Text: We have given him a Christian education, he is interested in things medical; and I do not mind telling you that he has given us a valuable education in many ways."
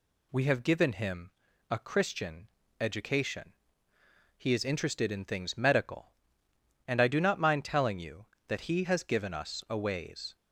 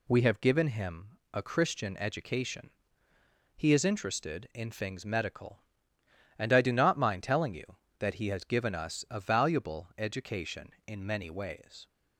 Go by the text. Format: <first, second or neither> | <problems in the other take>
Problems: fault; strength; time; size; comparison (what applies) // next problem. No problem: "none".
second | pauses between "him" and "a"; at 1.3 s; 0.40 s long; slight in the second // pauses between "Christian" and "education"; slight; at 2.4 s; 0.30 s long // skips "valuable education in many"; at 9.7 s